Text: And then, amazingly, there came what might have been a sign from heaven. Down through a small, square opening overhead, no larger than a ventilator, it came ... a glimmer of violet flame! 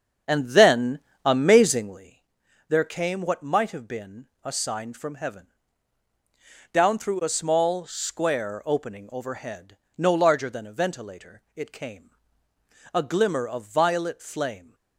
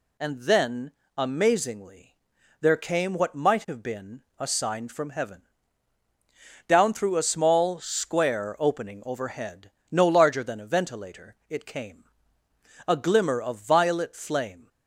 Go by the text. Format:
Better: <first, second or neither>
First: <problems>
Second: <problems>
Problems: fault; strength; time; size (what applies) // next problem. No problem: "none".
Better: second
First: starts louder than the rest; strong; until 2.2 s; 7.5 dB // pauses between "been" and "a"; slight; at 4.2 s; 0.16 s long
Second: pauses between "been" and "a"; slight; at 4.2 s; 0.16 s long